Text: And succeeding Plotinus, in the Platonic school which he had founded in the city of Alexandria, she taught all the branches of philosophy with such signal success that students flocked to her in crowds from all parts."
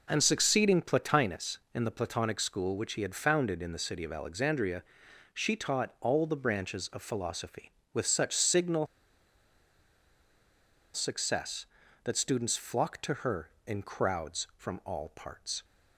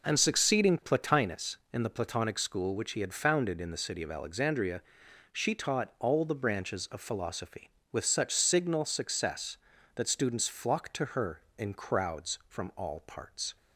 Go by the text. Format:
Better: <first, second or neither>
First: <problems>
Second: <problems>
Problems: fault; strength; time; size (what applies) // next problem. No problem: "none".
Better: second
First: pauses between "signal" and "success"; strong; at 8.8 s; 2.0 s long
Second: none